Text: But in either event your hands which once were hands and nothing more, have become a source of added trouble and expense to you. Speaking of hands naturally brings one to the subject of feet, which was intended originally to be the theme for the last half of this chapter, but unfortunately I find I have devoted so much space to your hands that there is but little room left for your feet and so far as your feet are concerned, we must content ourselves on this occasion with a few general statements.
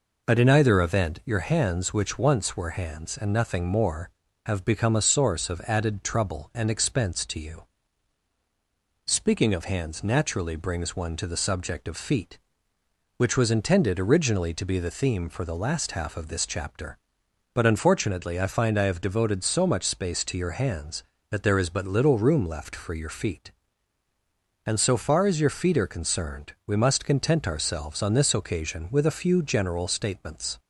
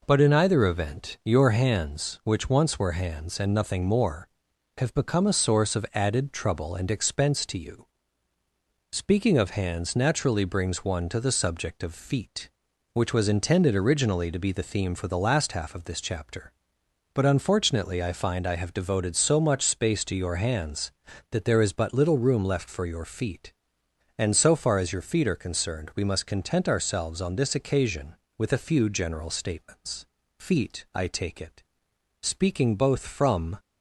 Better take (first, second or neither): first